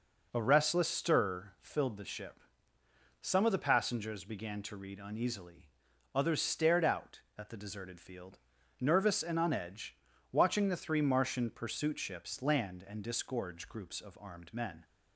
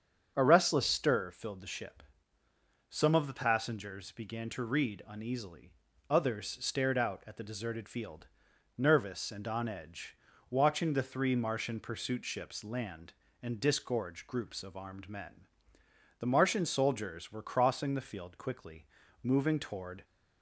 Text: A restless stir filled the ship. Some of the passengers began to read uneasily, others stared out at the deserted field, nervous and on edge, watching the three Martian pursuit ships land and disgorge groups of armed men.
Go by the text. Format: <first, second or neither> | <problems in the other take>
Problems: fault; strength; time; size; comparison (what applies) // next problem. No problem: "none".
first | starts louder than the rest; strong; until 1.3 s; 7.5 dB // goes on to say "The Martian soldiers were crossing the field quickly moving toward"; strong; from 16.1 s on; 3.8 s long